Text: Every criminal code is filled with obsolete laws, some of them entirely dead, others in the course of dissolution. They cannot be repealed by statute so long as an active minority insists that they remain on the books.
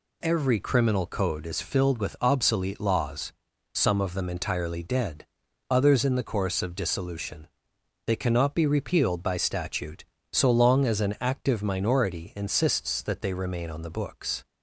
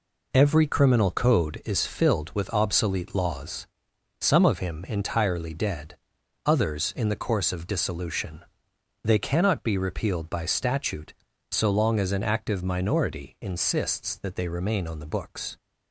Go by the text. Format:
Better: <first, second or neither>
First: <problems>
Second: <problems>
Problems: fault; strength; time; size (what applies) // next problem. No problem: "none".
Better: first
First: none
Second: says "him" for "them"; at 4.5 s